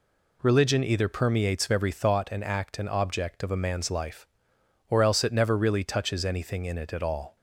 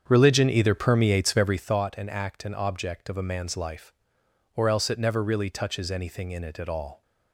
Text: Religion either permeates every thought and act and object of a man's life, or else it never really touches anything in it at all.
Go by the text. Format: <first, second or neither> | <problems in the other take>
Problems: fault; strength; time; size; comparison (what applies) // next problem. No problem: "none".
first | starts louder than the rest; strong; until 1.7 s; 7.5 dB